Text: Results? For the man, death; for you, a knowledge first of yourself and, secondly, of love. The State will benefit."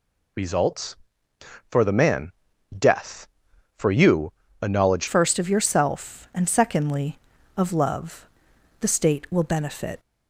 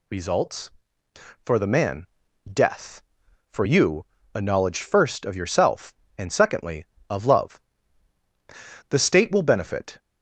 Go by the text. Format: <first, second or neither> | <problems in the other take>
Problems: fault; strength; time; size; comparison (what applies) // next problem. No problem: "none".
second | changes voice at "first"; from 5.0 s on; 4.9 s long